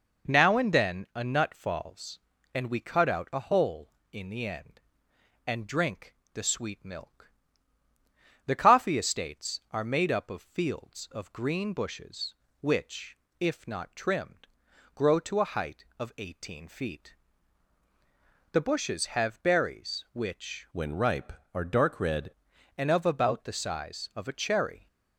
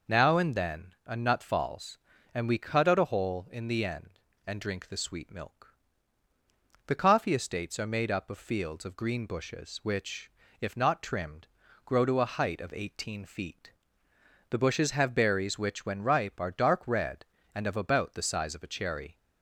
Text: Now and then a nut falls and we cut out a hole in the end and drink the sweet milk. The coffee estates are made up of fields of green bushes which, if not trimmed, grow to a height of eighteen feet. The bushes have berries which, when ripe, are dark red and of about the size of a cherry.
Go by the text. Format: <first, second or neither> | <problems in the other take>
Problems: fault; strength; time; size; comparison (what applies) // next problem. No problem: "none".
second | pauses between "drink" and "the"; slight; at 6.1 s; 0.18 s long // changes voice from "when" to "red"; from 20.7 to 22.2 s; 1.5 s long